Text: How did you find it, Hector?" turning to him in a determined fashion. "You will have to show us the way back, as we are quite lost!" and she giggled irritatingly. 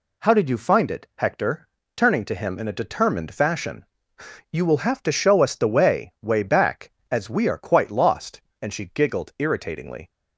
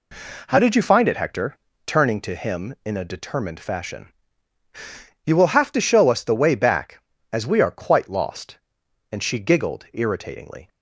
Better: second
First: says "way" twice; at 6.2 s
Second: none

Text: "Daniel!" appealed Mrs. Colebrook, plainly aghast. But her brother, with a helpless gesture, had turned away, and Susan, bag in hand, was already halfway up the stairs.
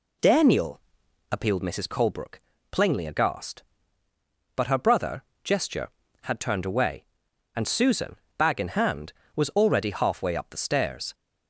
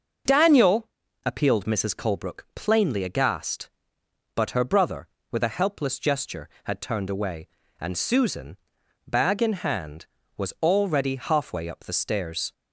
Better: second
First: skips "with a helpless"; at 5.3 s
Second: none

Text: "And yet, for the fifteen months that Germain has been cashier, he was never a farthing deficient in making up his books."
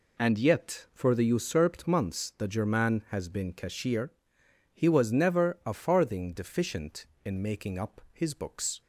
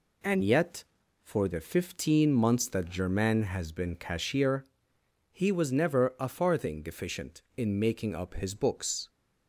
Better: second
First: says "usurped" for "fifteen"; at 1.2 s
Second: none

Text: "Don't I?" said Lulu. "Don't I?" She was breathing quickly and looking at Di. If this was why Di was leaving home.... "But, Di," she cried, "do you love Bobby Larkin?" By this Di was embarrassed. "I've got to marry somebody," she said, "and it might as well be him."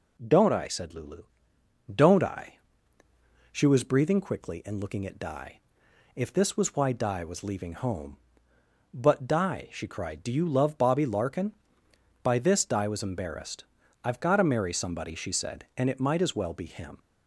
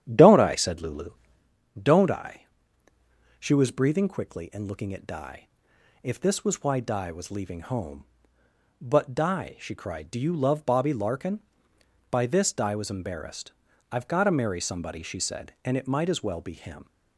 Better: first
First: none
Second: starts louder than the rest; strong; until 1.5 s; 10 dB

